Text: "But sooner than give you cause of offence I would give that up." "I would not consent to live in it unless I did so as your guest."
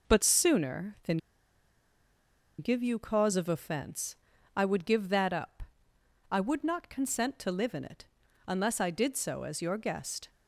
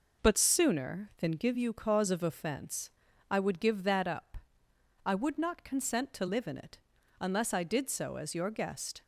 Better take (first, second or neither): second